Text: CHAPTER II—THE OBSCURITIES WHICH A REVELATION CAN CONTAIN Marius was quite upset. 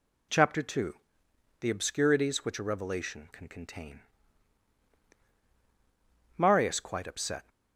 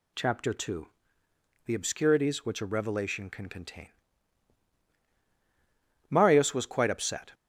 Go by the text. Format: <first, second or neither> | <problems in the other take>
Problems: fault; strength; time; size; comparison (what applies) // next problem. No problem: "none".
second | pauses between "CONTAIN" and "Marius"; strong; at 4.0 s; 2.3 s long; strong in the second // skips "was"; at 6.8 s